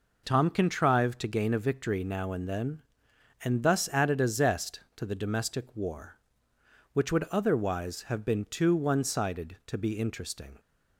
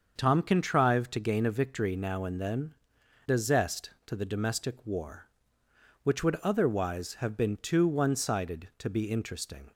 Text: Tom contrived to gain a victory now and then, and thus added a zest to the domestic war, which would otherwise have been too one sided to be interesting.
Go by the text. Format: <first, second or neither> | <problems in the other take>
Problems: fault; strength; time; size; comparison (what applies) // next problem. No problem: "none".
first | starts louder than the rest; until 1.1 s; 6.5 dB // skips "and thus added"; at 3.0 s